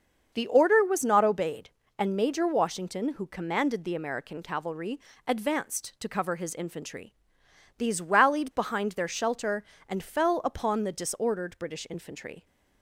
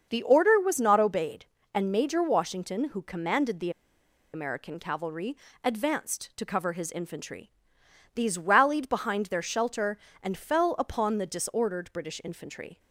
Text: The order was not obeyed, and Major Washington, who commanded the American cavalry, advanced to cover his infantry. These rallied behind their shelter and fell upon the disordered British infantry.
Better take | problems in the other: first | starts louder than the rest; until 1.1 s; 6.5 dB; also in the first // pauses between "the" and "American"; noticeable; at 3.6 s; 0.63 s long

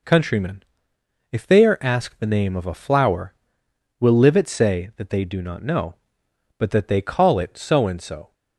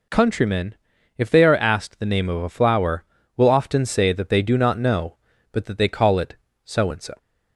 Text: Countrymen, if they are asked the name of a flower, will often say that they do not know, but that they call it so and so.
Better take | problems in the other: second | says "livet" for "often"; at 4.1 s

